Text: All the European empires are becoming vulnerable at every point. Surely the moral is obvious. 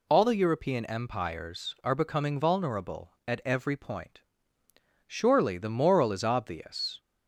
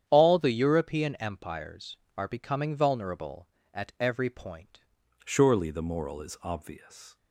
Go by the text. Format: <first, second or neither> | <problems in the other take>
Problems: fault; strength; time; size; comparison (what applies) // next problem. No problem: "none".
first | starts louder than the rest; strong; until 1.0 s; 9 dB // changes voice at "Surely"; from 5.2 s on; 1.9 s long